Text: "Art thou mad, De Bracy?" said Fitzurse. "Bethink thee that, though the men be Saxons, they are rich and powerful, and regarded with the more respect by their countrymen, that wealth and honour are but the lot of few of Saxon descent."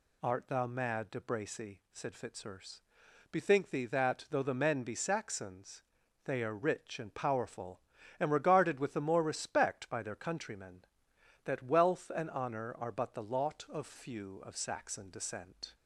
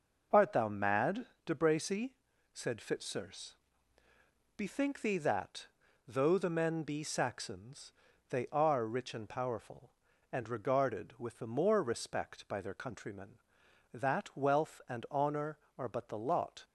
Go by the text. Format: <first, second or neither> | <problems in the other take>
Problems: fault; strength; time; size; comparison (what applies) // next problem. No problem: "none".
first | stops before "of few of Saxon descent"; at 16.6 s